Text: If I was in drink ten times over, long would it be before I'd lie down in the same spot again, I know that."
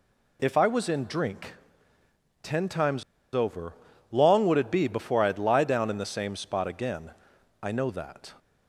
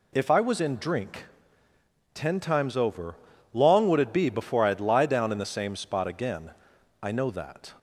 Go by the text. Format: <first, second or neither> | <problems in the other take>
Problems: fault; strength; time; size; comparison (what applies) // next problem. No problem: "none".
second | pauses between "drink" and "ten"; noticeable; at 1.5 s; 0.88 s long; noticeable in the second // pauses between "times" and "over"; slight; at 3.0 s; 0.30 s long